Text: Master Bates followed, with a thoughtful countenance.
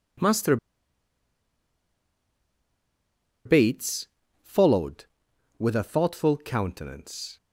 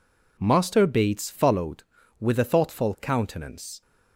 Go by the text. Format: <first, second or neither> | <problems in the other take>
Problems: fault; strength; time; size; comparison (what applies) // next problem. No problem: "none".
second | pauses between "Master" and "Bates"; strong; at 0.5 s; 2.8 s long // pauses between "Bates" and "followed"; slight; at 4.0 s; 0.36 s long